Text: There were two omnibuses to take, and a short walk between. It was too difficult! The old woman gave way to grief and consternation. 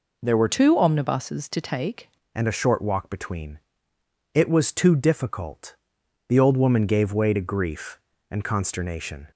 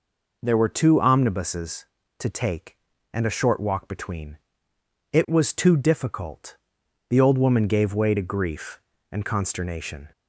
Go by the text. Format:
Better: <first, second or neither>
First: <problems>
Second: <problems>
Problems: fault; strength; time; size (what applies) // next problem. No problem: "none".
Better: second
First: changes voice from "two" to "take"; from 0.4 to 2.0 s; 1.6 s long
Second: none